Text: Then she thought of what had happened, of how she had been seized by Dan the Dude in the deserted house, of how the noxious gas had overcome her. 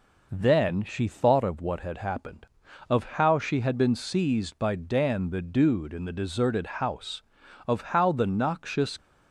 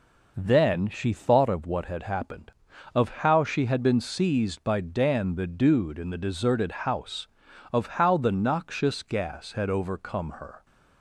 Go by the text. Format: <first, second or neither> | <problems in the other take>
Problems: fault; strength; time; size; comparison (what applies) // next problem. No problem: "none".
second | stops before "gas had overcome her"; at 8.9 s